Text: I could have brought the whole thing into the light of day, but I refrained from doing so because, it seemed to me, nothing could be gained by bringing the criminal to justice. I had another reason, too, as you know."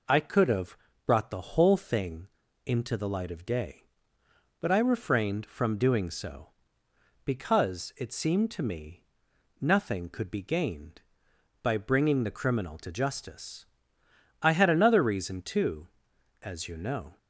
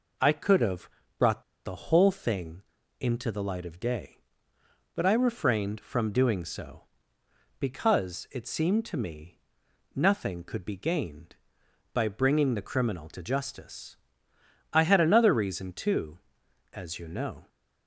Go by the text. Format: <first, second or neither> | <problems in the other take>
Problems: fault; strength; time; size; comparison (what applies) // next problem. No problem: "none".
first | pauses between "have" and "brought"; slight; at 0.8 s; 0.30 s long; slight in the first // pauses between "brought" and "the"; slight; at 1.4 s; 0.22 s long // pauses between "thing" and "into"; at 2.6 s; 0.38 s long; also in the first